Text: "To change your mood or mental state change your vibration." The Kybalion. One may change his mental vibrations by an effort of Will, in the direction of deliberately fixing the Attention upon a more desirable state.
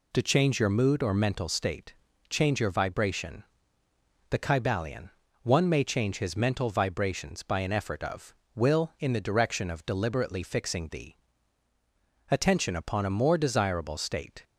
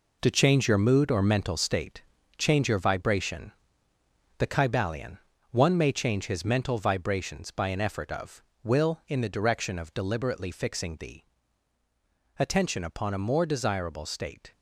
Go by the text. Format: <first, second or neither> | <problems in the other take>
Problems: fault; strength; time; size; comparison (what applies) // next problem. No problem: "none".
first | gets quieter; strong; throughout; 8.5 dB // pauses between "state" and "change"; slight; at 2.0 s; 0.36 s long; slight in the first // pauses between "the" and "Attention"; at 11.2 s; 1.1 s long; also in the first